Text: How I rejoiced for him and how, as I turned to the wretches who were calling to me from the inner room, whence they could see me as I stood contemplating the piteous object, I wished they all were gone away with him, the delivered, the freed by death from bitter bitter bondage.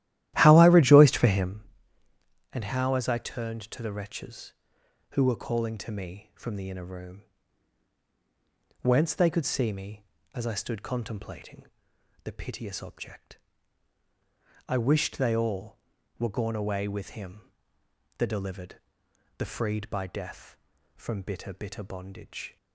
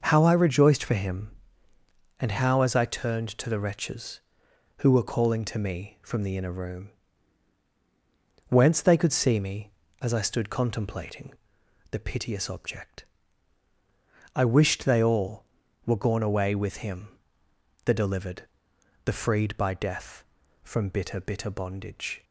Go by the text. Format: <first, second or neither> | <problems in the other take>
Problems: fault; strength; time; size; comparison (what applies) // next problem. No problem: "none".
second | starts louder than the rest; strong; until 1.5 s; 14 dB // pauses between "contemplating" and "the"; noticeable; at 11.6 s; 0.58 s long; noticeable in the second